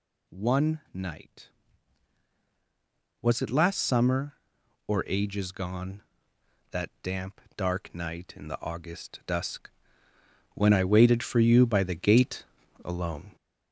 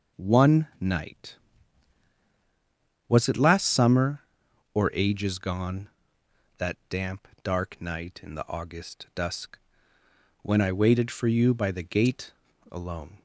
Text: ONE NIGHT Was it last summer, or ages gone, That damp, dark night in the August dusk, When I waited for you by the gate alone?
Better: second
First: gets louder; noticeable; throughout; 4 dB // pauses between "gate" and "alone"; at 12.4 s; 0.40 s long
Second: pauses between "gate" and "alone"; at 12.3 s; 0.38 s long

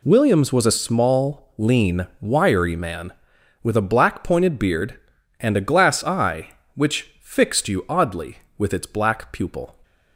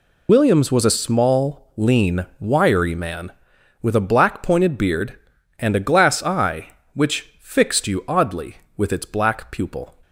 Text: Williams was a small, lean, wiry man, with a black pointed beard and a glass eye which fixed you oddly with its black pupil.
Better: first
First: none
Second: loses the start of "Williams"; at 0.2 s; 70 ms

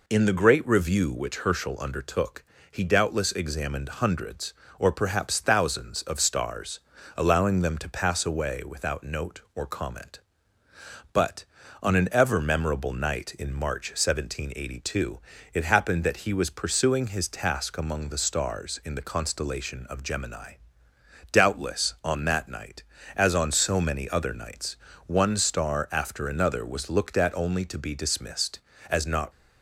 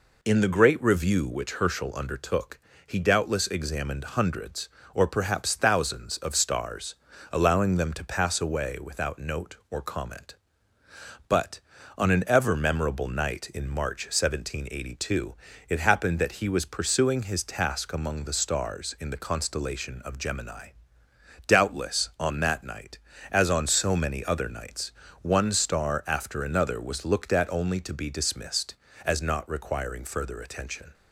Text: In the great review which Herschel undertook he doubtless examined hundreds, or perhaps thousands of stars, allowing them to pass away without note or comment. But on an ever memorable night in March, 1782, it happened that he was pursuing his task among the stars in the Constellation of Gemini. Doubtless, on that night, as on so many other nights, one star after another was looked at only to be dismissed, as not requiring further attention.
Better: second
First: pauses between "undertook" and "he"; slight; at 2.4 s; 0.26 s long // stops before "requiring further attention"; at 29.3 s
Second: pauses between "undertook" and "he"; slight; at 2.5 s; 0.26 s long

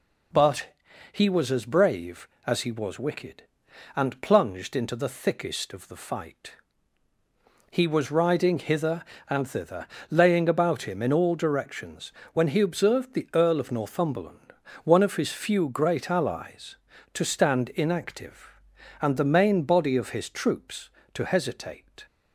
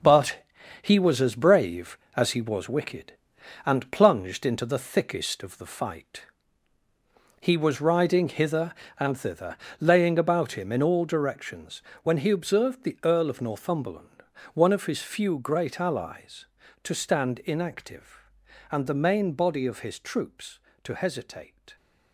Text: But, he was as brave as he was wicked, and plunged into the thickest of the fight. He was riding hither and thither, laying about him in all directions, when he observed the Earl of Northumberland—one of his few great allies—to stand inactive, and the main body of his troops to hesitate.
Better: first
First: none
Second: gets quieter; strong; throughout; 8 dB

